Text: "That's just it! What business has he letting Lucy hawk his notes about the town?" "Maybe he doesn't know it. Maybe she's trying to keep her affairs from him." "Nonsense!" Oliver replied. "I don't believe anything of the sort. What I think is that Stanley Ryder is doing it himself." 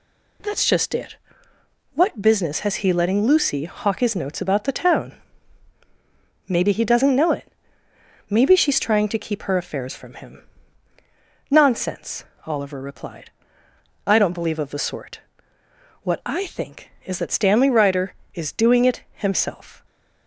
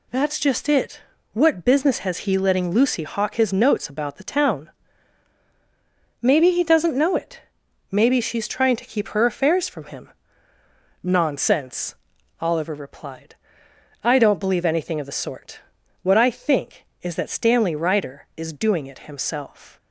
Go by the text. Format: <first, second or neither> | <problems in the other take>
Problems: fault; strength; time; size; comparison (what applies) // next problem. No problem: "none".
second | skips "anything"; at 14.5 s